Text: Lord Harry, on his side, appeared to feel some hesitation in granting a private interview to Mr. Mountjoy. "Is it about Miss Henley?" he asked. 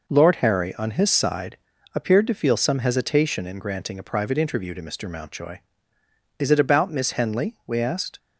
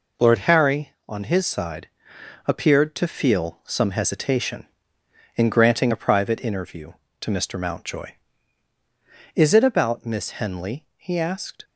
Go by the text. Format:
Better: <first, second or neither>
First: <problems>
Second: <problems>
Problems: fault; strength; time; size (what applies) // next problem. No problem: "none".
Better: second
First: says "we" for "he"; at 7.6 s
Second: none